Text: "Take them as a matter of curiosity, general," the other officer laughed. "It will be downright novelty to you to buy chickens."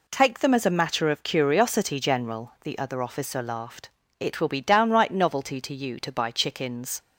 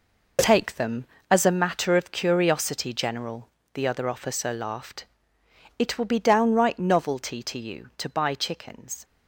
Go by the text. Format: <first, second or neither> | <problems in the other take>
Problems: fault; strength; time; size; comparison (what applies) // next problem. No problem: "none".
first | gets quieter; strong; throughout; 9.5 dB